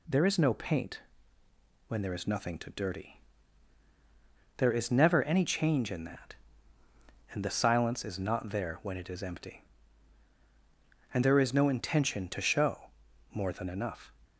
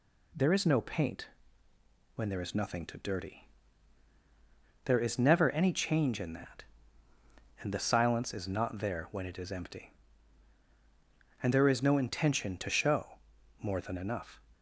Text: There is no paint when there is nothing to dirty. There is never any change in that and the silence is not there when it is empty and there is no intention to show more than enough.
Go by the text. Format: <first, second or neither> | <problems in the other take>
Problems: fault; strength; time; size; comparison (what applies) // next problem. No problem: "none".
neither | pauses between "paint" and "when"; noticeable; the same in both // pauses between "show" and "more"; the same in both